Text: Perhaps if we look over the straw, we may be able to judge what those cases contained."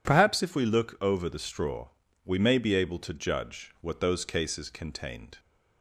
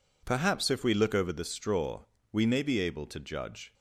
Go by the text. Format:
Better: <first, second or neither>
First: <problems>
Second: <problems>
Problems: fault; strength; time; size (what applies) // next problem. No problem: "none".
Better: first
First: none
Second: stops before "what those cases contained"; at 3.7 s